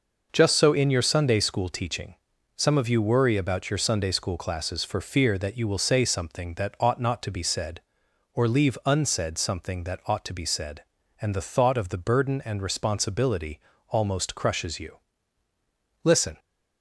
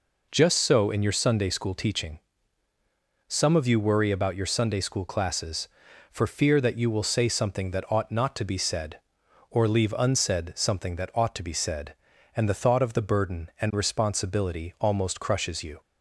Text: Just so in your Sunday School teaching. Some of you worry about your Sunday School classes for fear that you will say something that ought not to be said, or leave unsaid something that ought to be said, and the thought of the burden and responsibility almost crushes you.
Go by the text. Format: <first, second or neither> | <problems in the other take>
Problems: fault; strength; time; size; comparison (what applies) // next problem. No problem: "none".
second | pauses between "responsibility" and "almost"; slight; at 13.5 s; 0.32 s long // goes on to say "Listen"; slight; from 16.0 s on; 0.36 s long